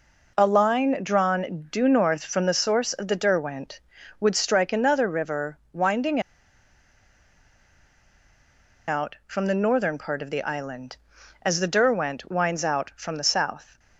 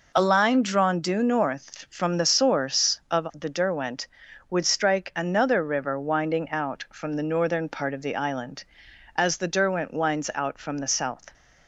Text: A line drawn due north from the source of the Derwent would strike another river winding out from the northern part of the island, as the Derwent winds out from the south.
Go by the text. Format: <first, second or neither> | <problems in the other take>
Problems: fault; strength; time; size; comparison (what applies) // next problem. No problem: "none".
second | pauses between "winding" and "out"; strong; at 6.1 s; 2.6 s long